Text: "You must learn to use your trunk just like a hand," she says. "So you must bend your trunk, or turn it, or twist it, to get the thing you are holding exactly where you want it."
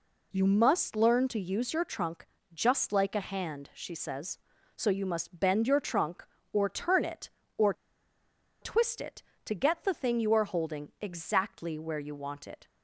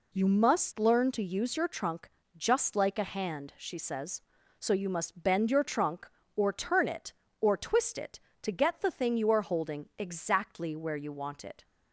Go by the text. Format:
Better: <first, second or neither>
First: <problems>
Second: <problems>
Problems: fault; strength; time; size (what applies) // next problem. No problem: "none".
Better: second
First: pauses between "trunk" and "just"; slight; at 2.2 s; 0.28 s long // pauses between "or" and "twist"; noticeable; at 7.7 s; 0.89 s long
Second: pauses between "trunk" and "just"; slight; at 2.0 s; 0.28 s long